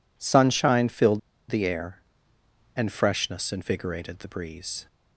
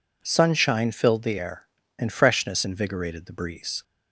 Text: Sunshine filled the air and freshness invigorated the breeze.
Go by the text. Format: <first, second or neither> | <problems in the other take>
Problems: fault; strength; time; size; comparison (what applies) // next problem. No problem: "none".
second | pauses between "filled" and "the"; slight; at 1.1 s; 0.28 s long